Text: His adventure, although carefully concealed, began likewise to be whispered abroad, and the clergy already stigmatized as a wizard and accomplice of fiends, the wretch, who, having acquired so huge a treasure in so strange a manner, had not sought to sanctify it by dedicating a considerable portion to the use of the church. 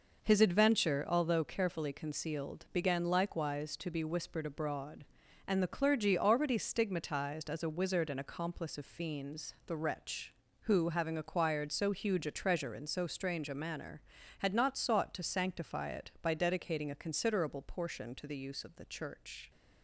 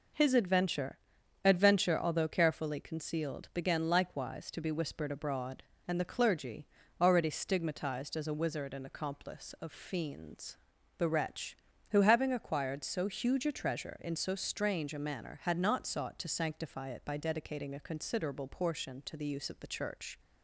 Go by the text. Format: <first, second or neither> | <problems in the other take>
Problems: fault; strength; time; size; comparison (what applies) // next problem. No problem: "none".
first | says "adventure" twice; at 1.4 s // pauses between "clergy" and "already"; slight; at 6.6 s; 0.34 s long